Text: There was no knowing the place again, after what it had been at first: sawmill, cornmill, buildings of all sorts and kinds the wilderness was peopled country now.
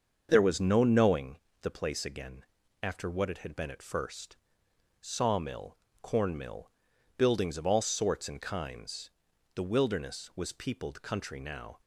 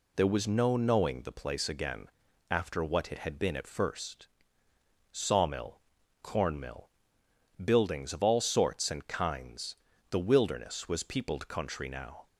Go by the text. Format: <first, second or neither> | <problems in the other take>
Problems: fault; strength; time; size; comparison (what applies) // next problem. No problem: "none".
second | starts louder than the rest; until 1.2 s; 6.5 dB // pauses between "knowing" and "the"; slight; at 1.3 s; 0.24 s long // pauses between "kinds" and "the"; noticeable; at 9.0 s; 0.46 s long; slight in the second